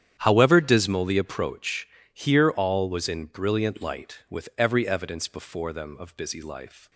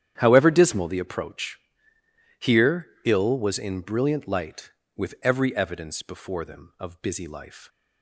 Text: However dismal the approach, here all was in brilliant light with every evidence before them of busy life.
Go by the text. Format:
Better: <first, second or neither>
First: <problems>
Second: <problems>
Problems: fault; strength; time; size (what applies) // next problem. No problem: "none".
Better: first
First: starts louder than the rest; strong; until 1.2 s; 9.5 dB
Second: starts louder than the rest; strong; until 1.1 s; 10 dB // says "ill" for "all"; at 3.0 s